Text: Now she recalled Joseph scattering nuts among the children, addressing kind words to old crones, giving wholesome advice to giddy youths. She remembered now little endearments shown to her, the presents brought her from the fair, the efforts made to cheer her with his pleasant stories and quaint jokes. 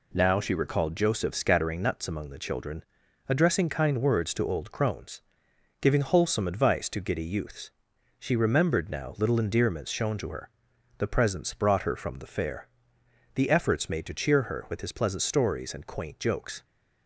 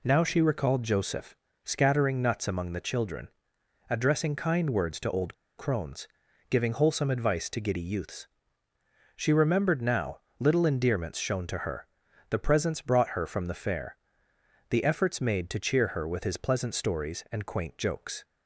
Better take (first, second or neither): first